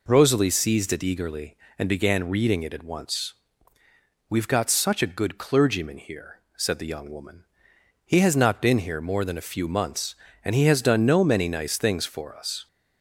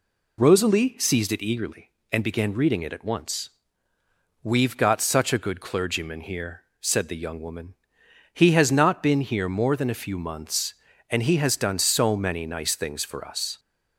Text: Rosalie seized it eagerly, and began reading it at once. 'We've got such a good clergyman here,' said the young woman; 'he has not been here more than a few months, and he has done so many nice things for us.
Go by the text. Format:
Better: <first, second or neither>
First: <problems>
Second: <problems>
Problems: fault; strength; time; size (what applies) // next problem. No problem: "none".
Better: second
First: says "no" for "so"; at 11.0 s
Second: none